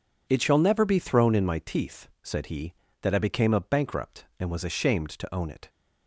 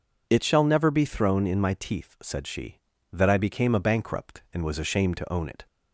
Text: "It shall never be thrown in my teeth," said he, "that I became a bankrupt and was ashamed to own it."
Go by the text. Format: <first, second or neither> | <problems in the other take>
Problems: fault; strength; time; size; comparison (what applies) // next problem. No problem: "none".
first | says "she" for "he"; at 2.4 s